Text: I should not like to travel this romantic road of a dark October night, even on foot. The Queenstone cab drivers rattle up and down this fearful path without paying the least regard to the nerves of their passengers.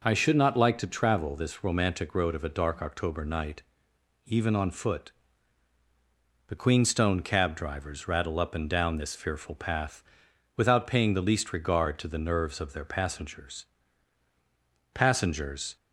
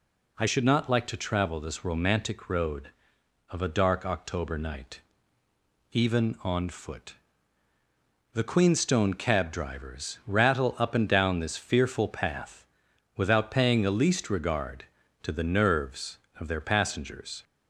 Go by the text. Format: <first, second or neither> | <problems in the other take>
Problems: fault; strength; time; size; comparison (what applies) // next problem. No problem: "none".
second | pauses between "path" and "without"; noticeable; at 10.0 s; 0.54 s long; noticeable in the second // says "passengers" twice; at 14.9 s